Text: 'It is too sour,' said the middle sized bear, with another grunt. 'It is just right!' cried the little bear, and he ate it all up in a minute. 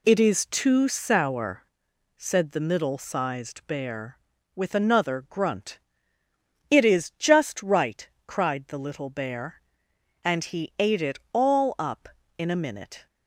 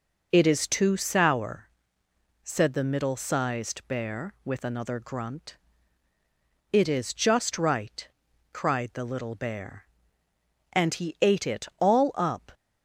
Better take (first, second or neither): first